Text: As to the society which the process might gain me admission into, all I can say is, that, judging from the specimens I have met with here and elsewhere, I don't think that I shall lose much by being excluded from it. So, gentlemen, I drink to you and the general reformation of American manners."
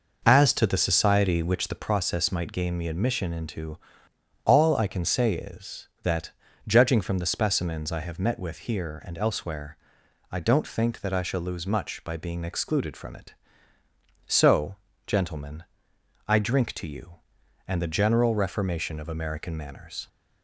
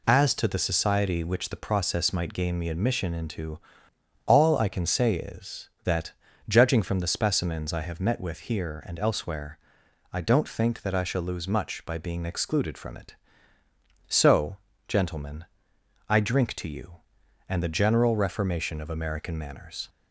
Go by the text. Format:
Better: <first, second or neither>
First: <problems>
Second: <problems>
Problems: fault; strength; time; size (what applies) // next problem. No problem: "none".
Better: second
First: starts louder than the rest; noticeable; until 2.0 s; 5.5 dB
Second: none